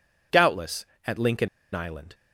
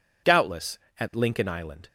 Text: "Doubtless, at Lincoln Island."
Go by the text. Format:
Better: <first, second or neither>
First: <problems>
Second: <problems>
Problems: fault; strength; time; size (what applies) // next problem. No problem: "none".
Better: second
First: pauses between "Lincoln" and "Island"; slight; at 1.4 s; 0.25 s long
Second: none